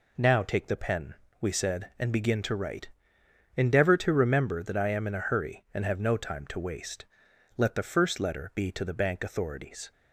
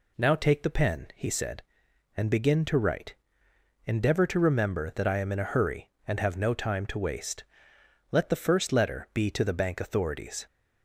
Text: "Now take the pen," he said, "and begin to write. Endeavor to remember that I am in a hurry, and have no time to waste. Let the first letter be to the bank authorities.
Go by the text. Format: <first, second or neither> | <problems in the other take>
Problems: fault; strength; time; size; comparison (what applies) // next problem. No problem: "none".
second | says "we" for "he"; at 1.3 s